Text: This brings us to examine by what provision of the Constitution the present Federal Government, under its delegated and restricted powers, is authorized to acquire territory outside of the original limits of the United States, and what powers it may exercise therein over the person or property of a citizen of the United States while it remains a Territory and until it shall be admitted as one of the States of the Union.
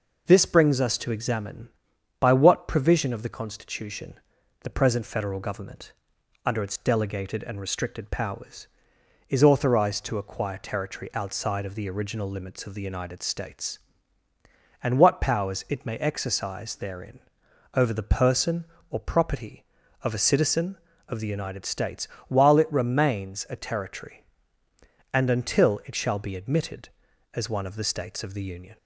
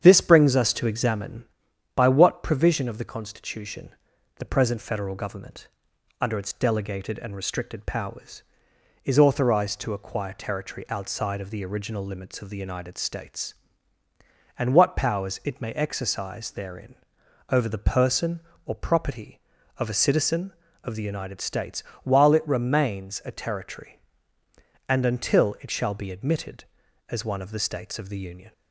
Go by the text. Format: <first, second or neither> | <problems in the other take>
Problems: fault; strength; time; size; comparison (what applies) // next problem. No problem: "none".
first | starts louder than the rest; strong; until 1.5 s; 8 dB // pauses between "Constitution" and "the"; noticeable; at 3.9 s; 0.50 s long; noticeable in the first // pauses between "therein" and "over"; noticeable; at 16.9 s; 0.54 s long; noticeable in the first // pauses between "States" and "while"; slight; at 21.8 s; 0.18 s long; slight in the first